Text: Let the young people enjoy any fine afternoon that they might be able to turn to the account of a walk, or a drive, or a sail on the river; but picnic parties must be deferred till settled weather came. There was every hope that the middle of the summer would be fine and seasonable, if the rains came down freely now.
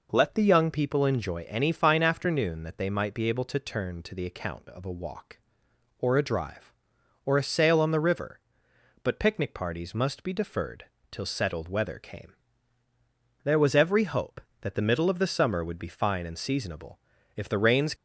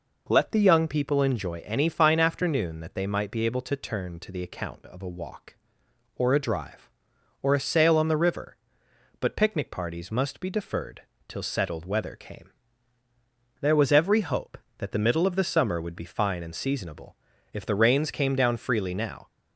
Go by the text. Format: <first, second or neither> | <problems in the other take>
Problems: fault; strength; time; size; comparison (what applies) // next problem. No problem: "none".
second | pauses between "deferred" and "till"; slight; at 10.8 s; 0.26 s long; slight in the second // stops before "came down freely now"; at 17.9 s